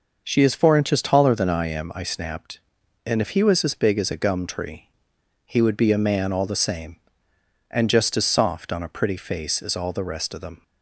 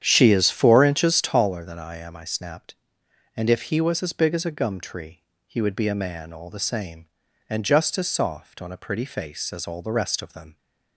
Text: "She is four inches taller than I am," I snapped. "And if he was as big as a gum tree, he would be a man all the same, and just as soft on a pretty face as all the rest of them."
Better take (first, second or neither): first